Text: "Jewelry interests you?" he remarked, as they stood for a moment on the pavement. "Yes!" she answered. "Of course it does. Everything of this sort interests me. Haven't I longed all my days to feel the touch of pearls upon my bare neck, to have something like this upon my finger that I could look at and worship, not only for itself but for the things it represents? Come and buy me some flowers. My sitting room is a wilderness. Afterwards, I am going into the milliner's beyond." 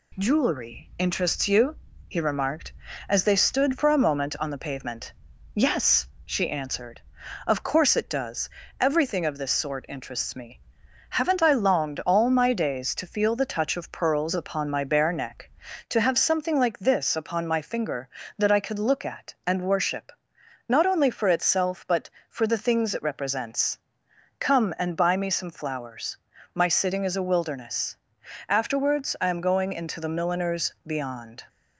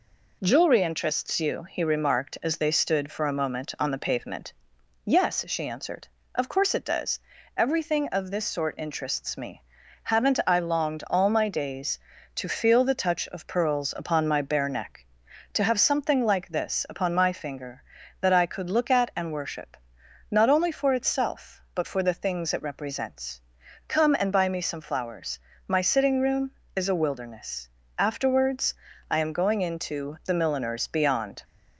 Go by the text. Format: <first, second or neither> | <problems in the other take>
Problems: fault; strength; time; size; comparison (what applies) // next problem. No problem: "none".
second | skips "room"; at 27.0 s